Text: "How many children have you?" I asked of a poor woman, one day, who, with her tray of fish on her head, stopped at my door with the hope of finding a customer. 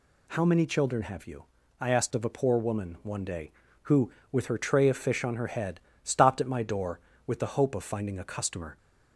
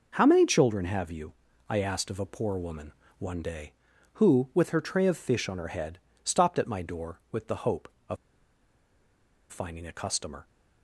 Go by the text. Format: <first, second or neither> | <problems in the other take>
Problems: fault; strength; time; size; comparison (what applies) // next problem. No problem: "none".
first | pauses between "of" and "finding"; strong; at 8.1 s; 1.3 s long